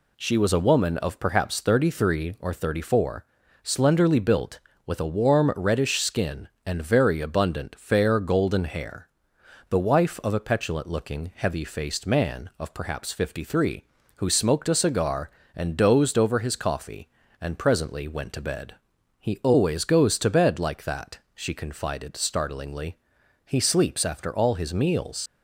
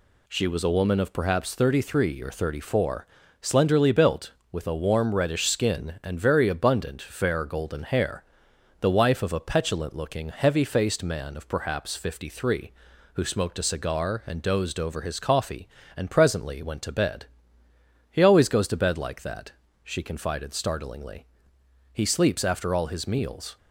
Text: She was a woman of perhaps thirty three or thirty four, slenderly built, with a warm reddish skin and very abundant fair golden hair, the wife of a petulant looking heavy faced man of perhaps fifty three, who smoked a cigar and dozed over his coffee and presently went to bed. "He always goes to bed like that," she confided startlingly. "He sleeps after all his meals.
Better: second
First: leaves "meals" unfinished; at 25.2 s; 75 ms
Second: none

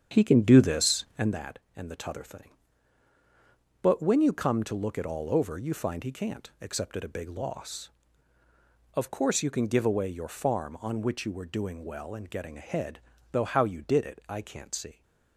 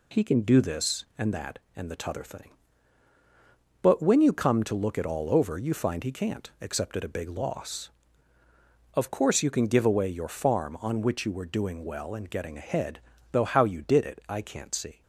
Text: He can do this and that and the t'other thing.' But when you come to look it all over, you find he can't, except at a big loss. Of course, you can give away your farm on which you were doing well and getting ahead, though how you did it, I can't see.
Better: second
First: starts louder than the rest; strong; until 1.4 s; 8 dB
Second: none

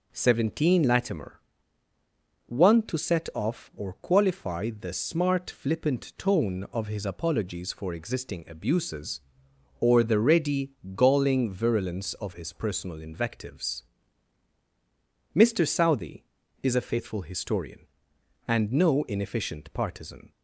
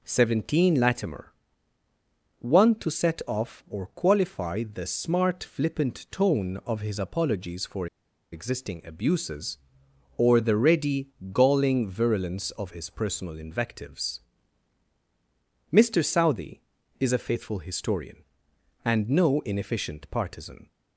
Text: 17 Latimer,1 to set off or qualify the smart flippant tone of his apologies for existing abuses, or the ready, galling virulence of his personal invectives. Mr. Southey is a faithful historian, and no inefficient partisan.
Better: first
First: none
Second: pauses between "for" and "existing"; noticeable; at 7.8 s; 0.46 s long

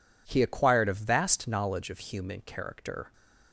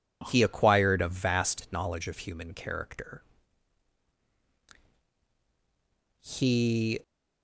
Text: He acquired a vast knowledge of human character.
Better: first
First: none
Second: goes on to say "He"; noticeable; from 6.2 s on; 0.80 s long

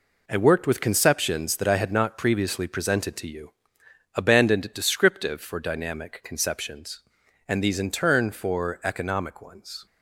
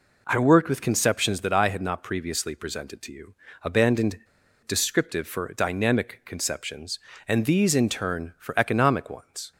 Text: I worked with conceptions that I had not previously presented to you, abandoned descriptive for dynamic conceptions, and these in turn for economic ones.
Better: first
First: none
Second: pauses between "abandoned" and "descriptive"; noticeable; at 4.2 s; 0.47 s long

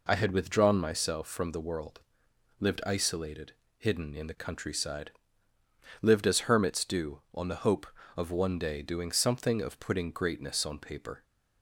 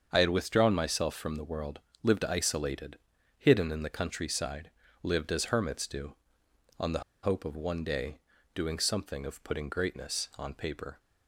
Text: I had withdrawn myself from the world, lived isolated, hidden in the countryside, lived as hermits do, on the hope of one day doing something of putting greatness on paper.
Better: first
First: none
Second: starts louder than the rest; until 1.1 s; 7 dB // pauses between "the" and "hope"; slight; at 7.0 s; 0.22 s long // pauses between "day" and "doing"; slight; at 8.1 s; 0.34 s long

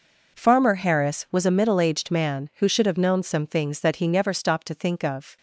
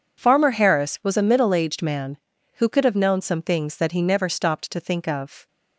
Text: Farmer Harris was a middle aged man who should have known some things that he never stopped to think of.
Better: first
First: none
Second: says "could" for "should"; at 2.6 s

